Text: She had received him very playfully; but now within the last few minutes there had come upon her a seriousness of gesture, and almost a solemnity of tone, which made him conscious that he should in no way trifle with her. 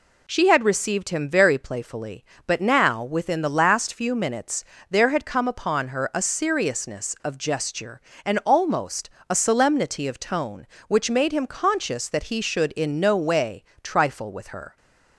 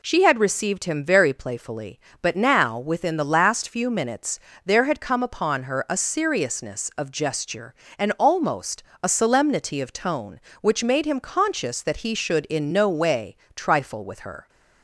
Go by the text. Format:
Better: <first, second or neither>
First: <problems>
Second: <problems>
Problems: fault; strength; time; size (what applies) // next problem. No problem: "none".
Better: neither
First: pauses between "minutes" and "there"; slight; at 4.6 s; 0.26 s long // pauses between "almost" and "a"; slight; at 9.0 s; 0.22 s long // pauses between "way" and "trifle"; slight; at 13.6 s; 0.20 s long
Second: pauses between "minutes" and "there"; slight; at 4.3 s; 0.26 s long // pauses between "almost" and "a"; slight; at 8.8 s; 0.22 s long // pauses between "way" and "trifle"; slight; at 13.3 s; 0.20 s long